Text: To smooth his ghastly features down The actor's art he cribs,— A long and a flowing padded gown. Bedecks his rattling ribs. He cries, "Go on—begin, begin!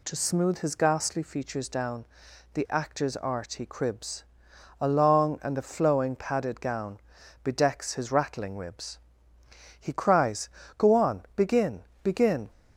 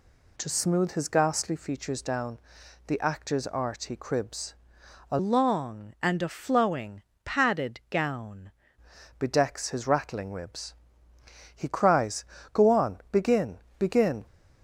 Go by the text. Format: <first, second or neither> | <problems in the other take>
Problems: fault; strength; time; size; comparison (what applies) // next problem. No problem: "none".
first | pauses between "down" and "The"; noticeable; at 2.3 s; 0.48 s long; noticeable in the first // changes voice from "long" to "gown"; from 5.1 to 8.5 s; 3.4 s long // pauses between "flowing" and "padded"; slight; at 7.0 s; 0.22 s long